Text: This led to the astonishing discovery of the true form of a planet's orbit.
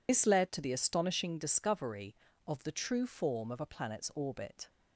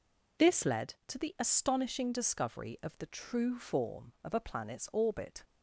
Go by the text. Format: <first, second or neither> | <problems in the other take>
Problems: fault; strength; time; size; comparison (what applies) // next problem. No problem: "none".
second | loses the start of "This"; at 0.0 s; 60 ms